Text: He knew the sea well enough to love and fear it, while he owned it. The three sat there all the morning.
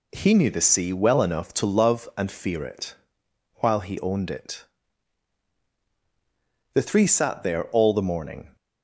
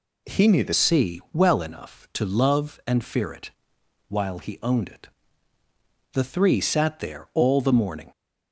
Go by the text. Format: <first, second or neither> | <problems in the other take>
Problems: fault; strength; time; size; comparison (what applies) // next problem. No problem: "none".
first | changes voice at "sea"; from 0.7 s on; 7.4 s long